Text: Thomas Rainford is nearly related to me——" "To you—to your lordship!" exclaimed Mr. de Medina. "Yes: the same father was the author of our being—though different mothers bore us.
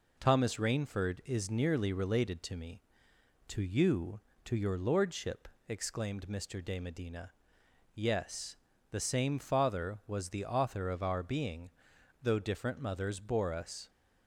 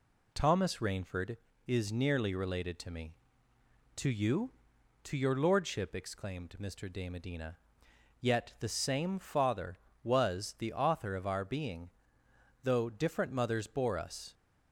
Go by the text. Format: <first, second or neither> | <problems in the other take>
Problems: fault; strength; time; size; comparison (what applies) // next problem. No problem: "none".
first | says "Yet" for "Yes"; at 8.2 s